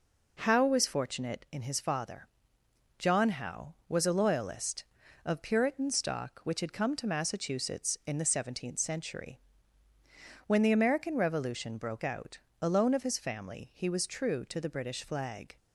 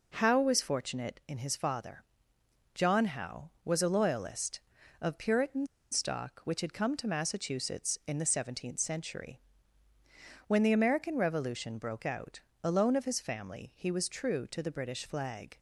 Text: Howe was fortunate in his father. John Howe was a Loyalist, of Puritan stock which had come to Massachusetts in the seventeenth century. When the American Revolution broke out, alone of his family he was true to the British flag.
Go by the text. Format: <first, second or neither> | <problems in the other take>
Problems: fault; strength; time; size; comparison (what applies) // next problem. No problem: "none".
first | pauses between "Puritan" and "stock"; slight; at 5.6 s; 0.26 s long